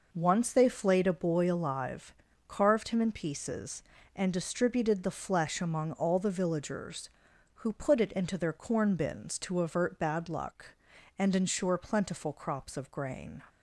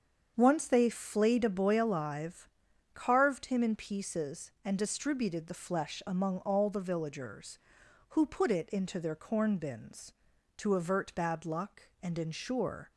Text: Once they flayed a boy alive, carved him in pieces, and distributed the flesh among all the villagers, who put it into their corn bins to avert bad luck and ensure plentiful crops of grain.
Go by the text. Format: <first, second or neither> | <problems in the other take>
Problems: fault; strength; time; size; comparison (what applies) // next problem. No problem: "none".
first | starts louder than the rest; until 1.3 s; 7 dB // stops before "plentiful crops of grain"; at 12.9 s